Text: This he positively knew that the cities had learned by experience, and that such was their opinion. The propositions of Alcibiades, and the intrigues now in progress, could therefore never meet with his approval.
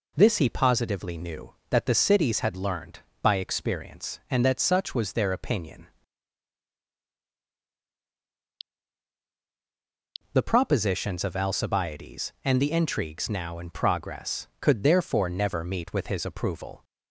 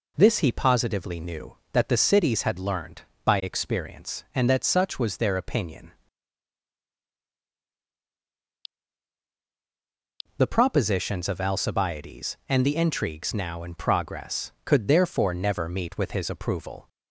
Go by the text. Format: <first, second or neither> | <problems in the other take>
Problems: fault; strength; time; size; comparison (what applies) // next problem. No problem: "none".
neither | none